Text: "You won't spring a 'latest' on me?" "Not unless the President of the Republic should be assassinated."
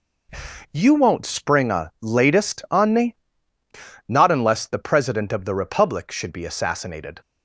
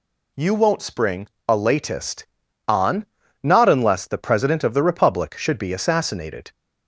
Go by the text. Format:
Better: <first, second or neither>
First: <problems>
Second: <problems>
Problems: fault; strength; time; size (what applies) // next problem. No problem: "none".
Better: first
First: none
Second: pauses between "spring" and "a"; slight; at 1.2 s; 0.20 s long // skips "me"; at 3.2 s